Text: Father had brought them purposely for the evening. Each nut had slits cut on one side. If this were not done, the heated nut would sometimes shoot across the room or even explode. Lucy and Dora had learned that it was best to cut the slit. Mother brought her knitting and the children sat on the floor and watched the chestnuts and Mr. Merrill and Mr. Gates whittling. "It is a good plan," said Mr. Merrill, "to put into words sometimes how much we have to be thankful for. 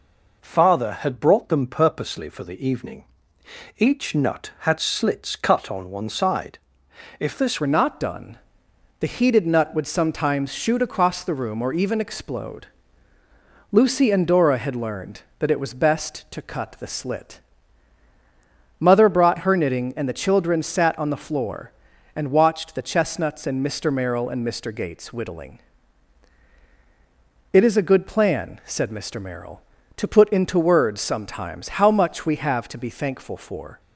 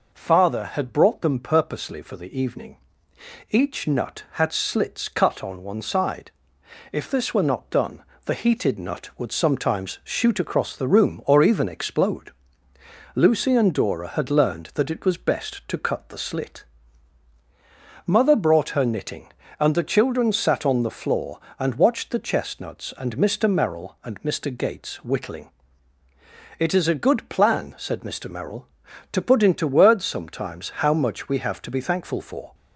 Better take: second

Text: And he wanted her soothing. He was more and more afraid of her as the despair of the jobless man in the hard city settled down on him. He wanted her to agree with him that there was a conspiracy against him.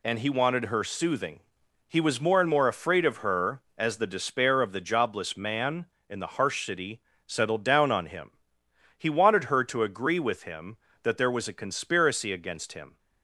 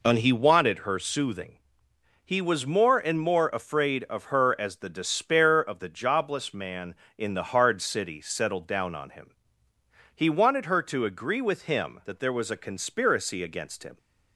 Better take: second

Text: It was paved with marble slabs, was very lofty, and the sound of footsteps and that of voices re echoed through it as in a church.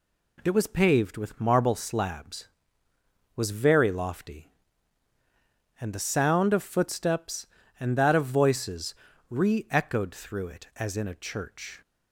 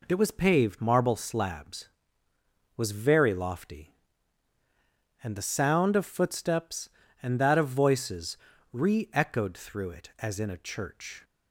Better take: first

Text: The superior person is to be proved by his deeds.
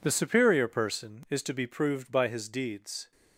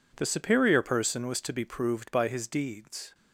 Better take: first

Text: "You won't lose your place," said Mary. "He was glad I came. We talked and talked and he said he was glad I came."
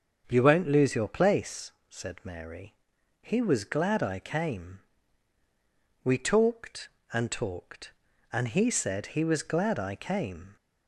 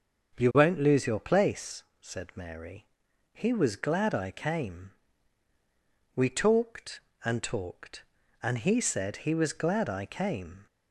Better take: neither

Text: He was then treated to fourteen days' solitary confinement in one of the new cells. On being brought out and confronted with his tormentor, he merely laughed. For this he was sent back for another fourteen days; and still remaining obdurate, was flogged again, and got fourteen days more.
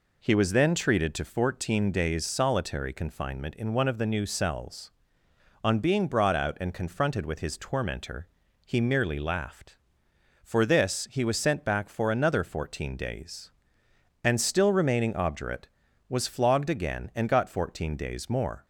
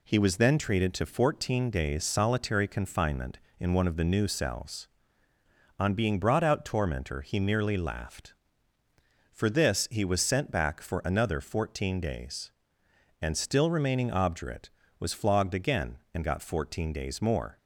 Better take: first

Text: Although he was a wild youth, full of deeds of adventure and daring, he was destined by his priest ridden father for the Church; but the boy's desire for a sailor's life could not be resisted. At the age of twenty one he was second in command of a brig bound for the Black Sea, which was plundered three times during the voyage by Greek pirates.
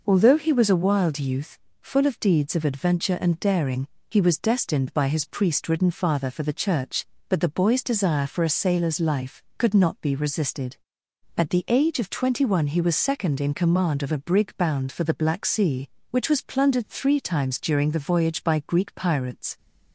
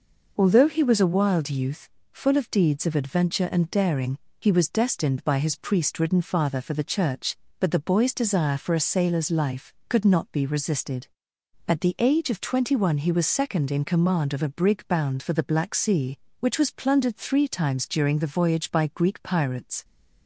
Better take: neither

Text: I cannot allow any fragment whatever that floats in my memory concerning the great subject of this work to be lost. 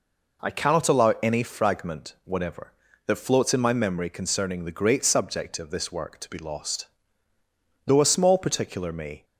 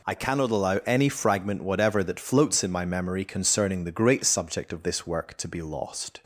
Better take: second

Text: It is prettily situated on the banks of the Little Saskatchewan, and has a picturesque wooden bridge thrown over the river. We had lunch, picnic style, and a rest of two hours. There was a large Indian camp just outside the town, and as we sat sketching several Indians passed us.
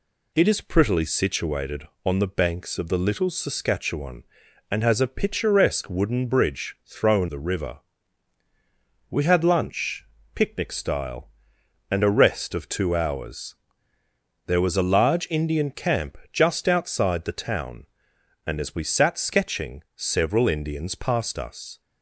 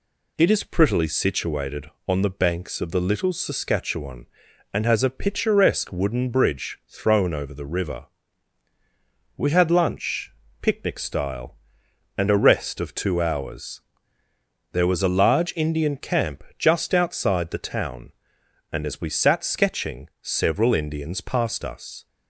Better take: second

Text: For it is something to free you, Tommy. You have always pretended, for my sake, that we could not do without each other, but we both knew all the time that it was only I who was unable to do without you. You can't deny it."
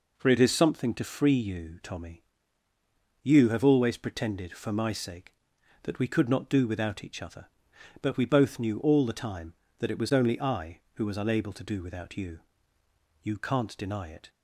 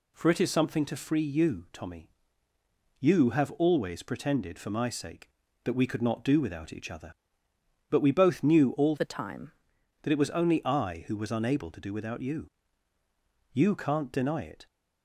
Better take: first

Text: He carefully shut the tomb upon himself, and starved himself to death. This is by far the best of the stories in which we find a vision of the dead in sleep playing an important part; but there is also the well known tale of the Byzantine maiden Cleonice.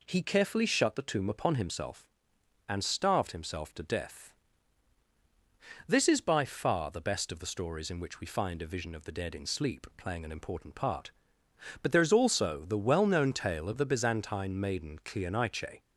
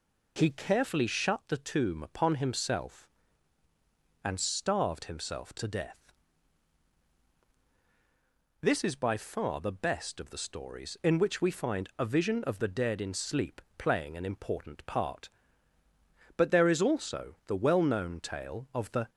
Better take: first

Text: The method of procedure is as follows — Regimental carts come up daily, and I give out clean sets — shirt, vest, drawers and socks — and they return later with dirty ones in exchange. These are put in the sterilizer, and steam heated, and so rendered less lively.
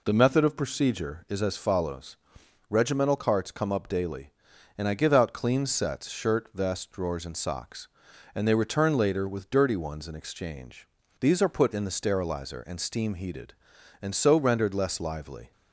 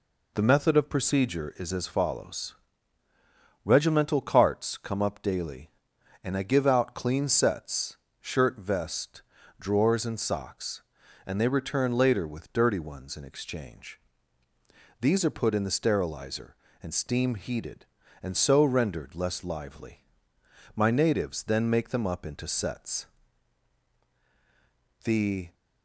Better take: first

